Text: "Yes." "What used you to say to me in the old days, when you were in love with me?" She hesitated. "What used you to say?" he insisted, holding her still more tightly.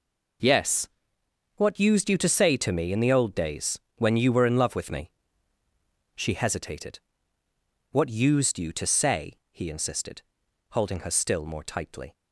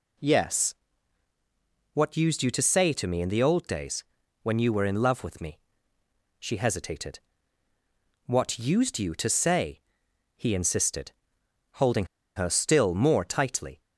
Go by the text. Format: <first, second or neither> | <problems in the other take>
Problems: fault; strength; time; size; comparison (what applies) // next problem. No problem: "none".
first | pauses between "holding" and "her"; slight; at 12.0 s; 0.30 s long